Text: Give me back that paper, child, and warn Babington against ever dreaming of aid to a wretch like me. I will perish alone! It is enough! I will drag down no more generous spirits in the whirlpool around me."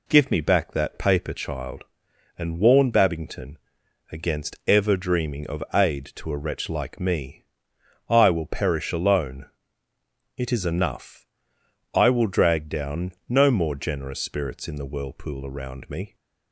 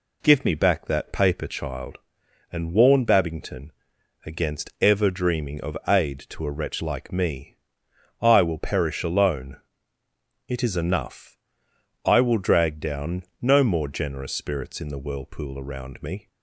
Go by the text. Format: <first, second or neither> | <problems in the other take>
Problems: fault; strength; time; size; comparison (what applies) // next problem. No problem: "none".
neither | pauses between "Babington" and "against"; noticeable; the same in both // pauses between "down" and "no"; slight; the same in both